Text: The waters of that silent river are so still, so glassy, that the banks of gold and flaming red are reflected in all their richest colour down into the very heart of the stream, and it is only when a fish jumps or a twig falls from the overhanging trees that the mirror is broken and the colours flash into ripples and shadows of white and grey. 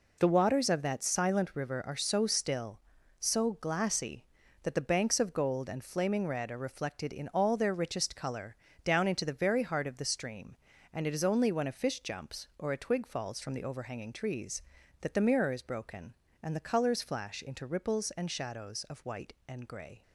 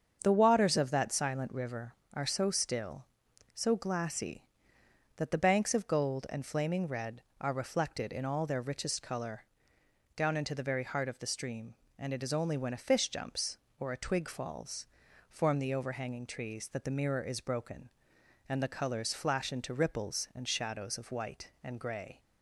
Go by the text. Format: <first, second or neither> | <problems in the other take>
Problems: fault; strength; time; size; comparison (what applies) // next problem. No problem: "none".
first | starts louder than the rest; strong; until 1.2 s; 7 dB // pauses between "colour" and "down"; noticeable; at 9.4 s; 0.72 s long; slight in the first // says "form" for "from"; at 15.2 s